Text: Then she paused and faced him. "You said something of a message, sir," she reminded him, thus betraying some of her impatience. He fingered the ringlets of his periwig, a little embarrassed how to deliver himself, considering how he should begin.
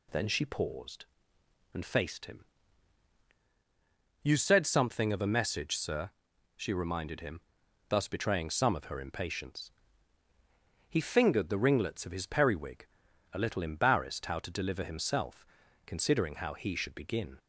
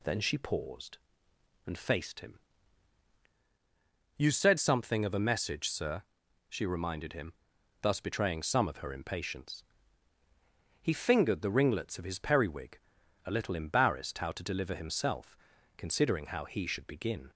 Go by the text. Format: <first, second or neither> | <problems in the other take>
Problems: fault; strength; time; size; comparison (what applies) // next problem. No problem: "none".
neither | none